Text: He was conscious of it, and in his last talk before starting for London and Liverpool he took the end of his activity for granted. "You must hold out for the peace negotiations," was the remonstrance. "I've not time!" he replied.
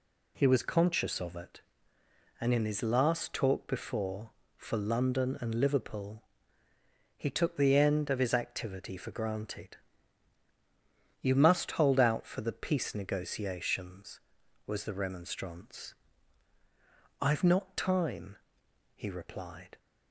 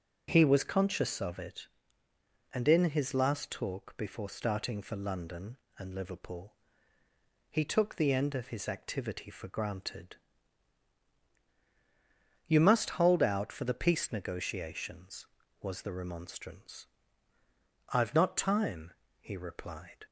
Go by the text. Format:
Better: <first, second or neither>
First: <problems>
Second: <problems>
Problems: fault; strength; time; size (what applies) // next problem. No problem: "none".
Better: second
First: skips "starting"; at 4.4 s // pauses between "Liverpool" and "he"; noticeable; at 6.2 s; 0.92 s long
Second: pauses between "Liverpool" and "he"; noticeable; at 6.5 s; 0.96 s long